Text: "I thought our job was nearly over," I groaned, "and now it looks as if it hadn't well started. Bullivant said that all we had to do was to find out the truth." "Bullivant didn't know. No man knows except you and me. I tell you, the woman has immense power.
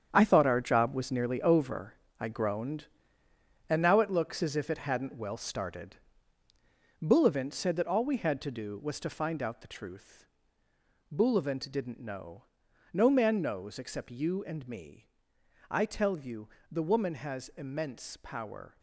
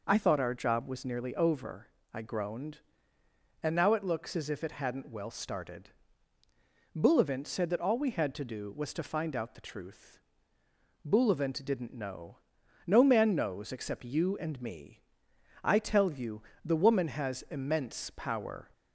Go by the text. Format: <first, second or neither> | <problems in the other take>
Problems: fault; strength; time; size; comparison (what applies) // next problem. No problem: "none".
second | gets quieter; strong; throughout; 11 dB